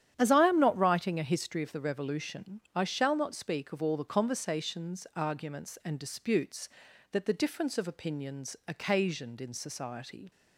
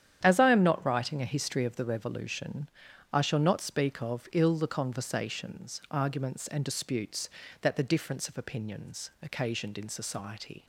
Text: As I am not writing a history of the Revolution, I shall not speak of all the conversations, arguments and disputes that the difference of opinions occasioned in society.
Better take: first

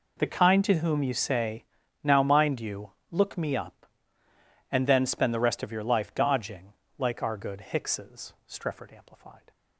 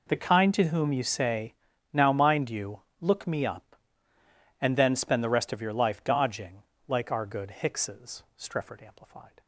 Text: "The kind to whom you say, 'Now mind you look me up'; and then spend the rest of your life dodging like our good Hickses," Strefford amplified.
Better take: neither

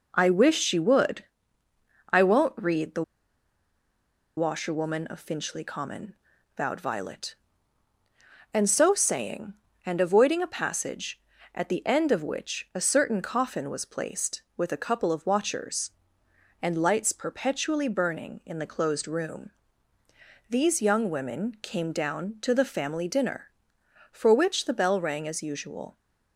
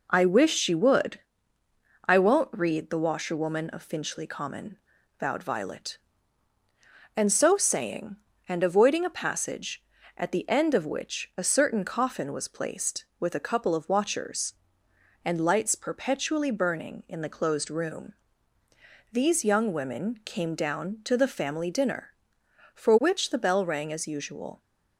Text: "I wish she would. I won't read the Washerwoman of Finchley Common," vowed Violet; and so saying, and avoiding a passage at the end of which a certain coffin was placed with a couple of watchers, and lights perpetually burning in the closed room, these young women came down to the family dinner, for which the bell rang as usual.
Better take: second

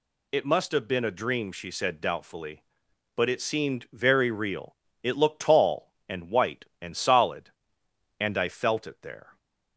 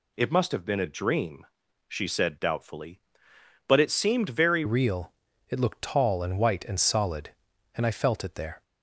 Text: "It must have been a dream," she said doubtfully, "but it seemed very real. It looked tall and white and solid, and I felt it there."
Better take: first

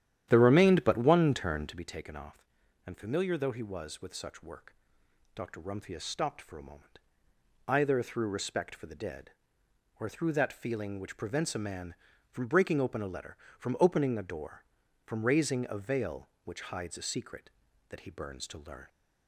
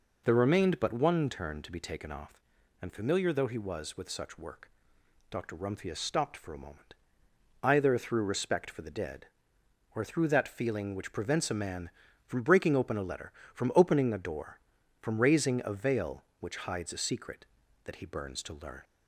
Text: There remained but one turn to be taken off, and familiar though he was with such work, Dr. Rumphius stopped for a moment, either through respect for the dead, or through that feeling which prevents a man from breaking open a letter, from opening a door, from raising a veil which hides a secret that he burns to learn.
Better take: second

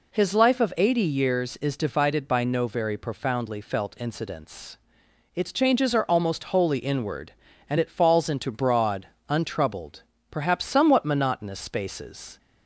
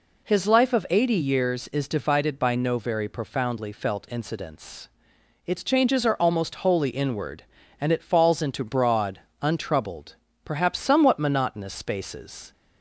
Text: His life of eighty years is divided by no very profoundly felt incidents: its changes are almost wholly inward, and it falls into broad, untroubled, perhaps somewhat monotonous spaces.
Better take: neither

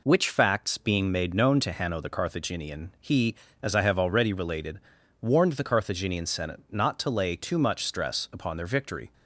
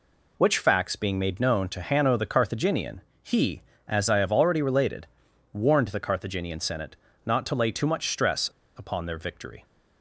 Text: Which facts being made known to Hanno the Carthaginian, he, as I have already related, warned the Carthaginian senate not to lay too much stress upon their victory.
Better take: first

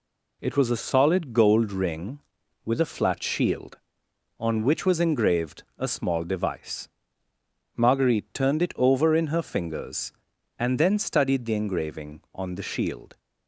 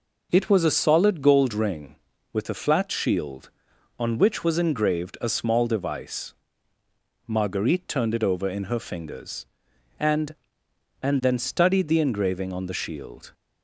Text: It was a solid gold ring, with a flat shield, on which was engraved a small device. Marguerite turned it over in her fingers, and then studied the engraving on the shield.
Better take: first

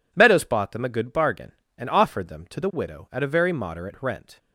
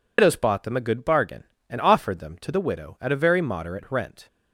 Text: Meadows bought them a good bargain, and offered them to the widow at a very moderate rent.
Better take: first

